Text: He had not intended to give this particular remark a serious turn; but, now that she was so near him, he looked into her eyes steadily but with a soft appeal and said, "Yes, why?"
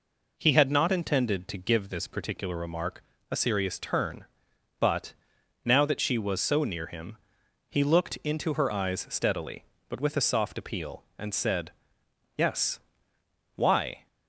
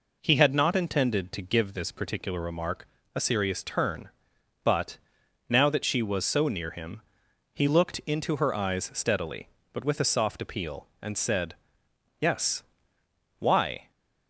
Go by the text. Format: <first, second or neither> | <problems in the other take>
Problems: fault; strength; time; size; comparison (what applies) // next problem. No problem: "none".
neither | pauses between "remark" and "a"; slight; the same in both